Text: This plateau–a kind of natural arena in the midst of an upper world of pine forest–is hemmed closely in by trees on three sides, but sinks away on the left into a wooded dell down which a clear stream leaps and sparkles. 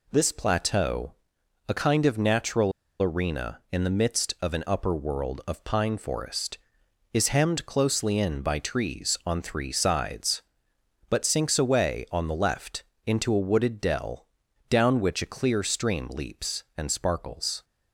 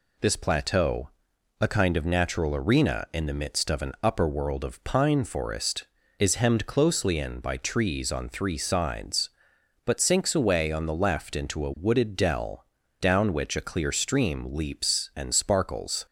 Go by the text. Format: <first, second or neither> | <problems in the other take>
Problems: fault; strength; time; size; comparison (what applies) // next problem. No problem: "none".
second | pauses between "natural" and "arena"; slight; at 2.7 s; 0.30 s long // pauses between "left" and "into"; slight; at 12.8 s; 0.22 s long // pauses between "dell" and "down"; at 14.2 s; 0.42 s long; slight in the second